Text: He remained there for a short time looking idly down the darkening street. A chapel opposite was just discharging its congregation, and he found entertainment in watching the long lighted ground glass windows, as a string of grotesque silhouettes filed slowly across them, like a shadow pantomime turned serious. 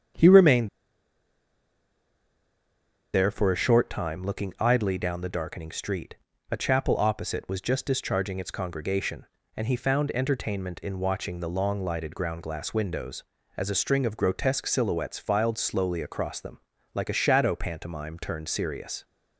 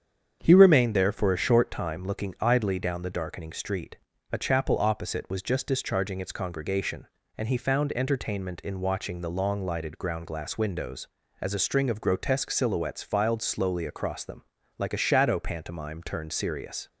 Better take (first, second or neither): second